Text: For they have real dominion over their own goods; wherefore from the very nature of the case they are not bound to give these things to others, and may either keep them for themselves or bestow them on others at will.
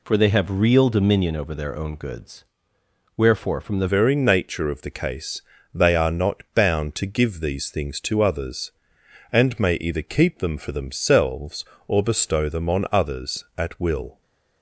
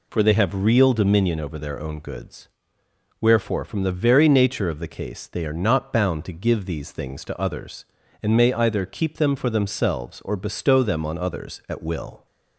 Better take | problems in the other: second | changes voice at "very"; from 3.8 s on; 10.4 s long // pauses between "case" and "they"; slight; at 5.4 s; 0.34 s long

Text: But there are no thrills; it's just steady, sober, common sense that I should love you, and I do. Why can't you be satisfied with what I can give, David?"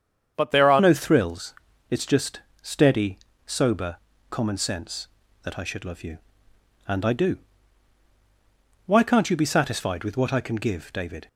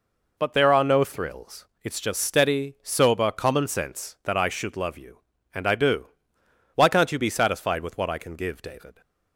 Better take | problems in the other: second | starts louder than the rest; strong; until 1.3 s; 7.5 dB // changes voice at "no"; from 0.7 s on; 10.5 s long // pauses between "just" and "steady"; slight; at 2.3 s; 0.24 s long

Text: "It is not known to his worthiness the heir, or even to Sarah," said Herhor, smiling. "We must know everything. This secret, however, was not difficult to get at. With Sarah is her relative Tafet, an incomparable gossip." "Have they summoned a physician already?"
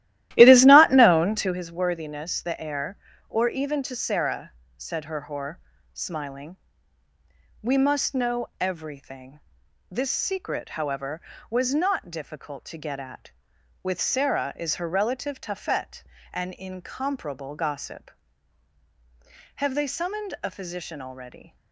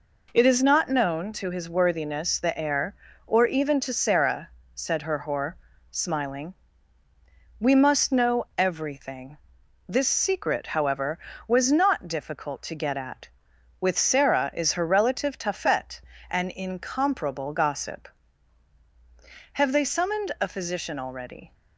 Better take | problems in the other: second | starts louder than the rest; strong; until 1.7 s; 14.5 dB

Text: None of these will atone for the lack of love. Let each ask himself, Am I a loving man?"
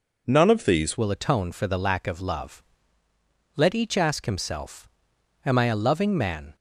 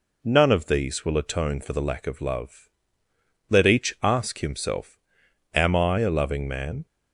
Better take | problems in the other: second | changes voice at "will"; from 0.9 s on; 5.6 s long

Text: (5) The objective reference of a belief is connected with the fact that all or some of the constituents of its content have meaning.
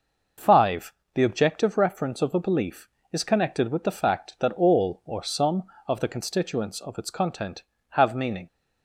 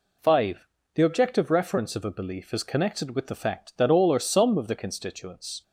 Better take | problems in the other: first | stops before "of its content have meaning"; at 5.6 s

